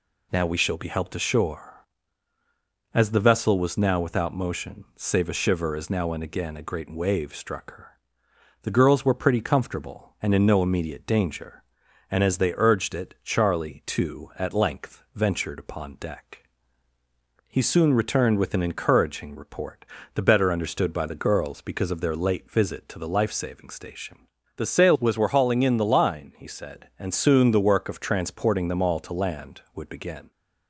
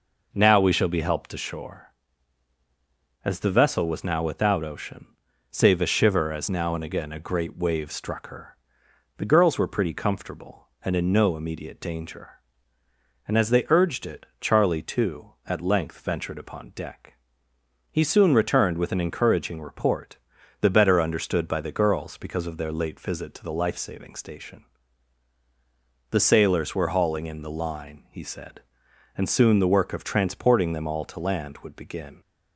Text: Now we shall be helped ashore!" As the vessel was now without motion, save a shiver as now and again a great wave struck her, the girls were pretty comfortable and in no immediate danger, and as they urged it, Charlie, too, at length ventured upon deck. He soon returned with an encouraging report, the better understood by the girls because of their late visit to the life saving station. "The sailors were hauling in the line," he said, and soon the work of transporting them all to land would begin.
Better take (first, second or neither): first